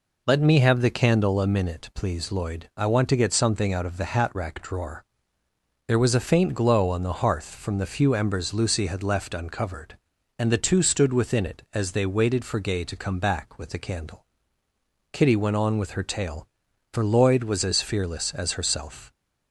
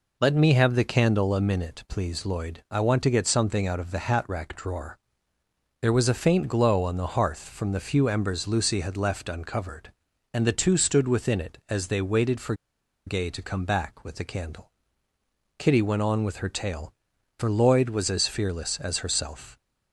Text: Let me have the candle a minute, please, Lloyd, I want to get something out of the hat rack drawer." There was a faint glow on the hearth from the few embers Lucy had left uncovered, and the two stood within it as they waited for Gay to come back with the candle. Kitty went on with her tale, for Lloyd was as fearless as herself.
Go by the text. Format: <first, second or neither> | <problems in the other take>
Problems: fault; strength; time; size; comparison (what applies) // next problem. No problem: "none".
first | pauses between "for" and "Gay"; noticeable; at 12.5 s; 0.52 s long